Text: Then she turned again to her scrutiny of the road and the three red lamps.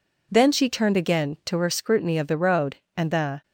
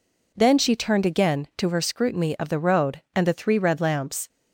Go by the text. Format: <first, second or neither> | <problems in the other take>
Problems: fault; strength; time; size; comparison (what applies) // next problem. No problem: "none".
second | stops before "three red lamps"; at 3.4 s